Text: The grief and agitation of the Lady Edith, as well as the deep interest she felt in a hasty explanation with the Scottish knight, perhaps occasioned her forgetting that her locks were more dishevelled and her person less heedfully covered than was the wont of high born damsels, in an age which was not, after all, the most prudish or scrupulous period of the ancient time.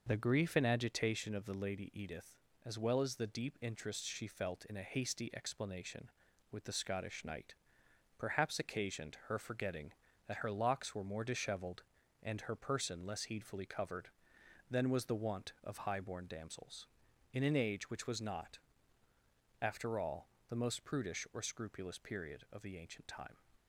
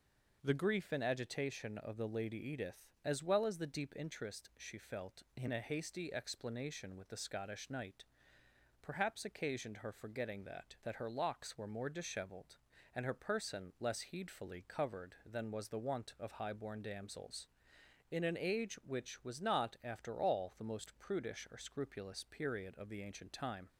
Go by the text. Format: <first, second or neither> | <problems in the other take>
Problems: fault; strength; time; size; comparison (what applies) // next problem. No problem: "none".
first | says "that" twice; at 10.8 s